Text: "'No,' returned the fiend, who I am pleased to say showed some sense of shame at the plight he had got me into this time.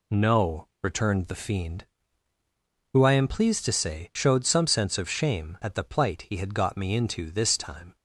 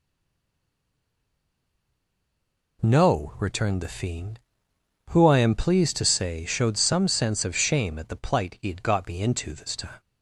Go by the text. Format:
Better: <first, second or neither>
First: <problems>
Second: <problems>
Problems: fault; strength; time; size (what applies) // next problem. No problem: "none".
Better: first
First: none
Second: stays silent before the first word; strong; until 2.8 s; 2.8 s long